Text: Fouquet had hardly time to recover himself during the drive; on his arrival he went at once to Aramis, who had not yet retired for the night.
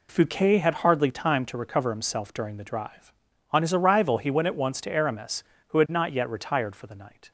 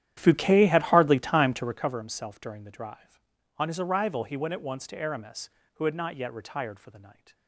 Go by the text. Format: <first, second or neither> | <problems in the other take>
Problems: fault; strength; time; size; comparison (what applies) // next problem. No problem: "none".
first | starts louder than the rest; strong; until 2.0 s; 11 dB